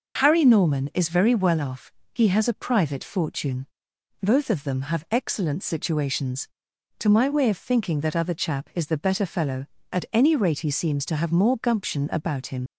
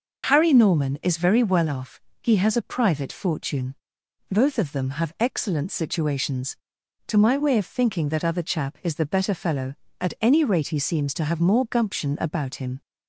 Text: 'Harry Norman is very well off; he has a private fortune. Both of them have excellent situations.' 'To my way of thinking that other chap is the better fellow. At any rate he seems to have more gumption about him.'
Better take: second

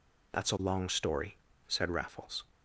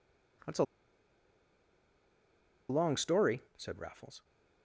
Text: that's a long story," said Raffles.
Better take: first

